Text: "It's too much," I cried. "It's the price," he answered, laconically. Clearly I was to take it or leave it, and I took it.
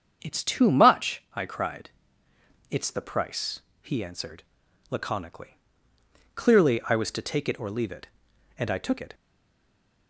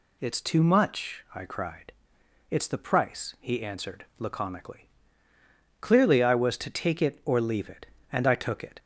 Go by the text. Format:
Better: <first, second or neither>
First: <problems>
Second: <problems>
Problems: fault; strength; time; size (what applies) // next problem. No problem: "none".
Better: second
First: starts louder than the rest; strong; until 1.2 s; 7.5 dB // stays silent after the last word; slight; from 9.1 s on; 0.9 s long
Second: none